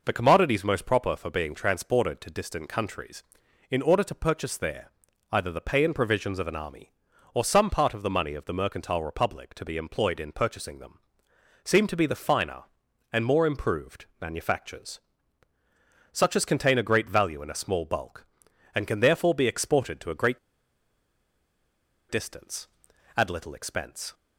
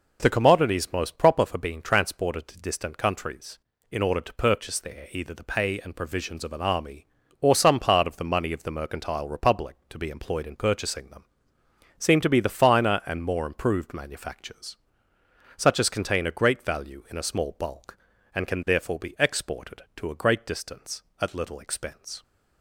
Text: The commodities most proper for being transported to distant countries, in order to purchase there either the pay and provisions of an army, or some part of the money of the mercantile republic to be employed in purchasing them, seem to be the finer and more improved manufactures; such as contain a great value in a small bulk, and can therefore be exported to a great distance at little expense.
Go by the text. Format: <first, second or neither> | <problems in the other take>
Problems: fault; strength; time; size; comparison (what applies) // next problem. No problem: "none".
second | pauses between "there" and "either"; at 4.8 s; 0.42 s long // pauses between "improved" and "manufactures"; slight; at 14.0 s; 0.16 s long // pauses between "great" and "distance"; strong; at 20.3 s; 1.7 s long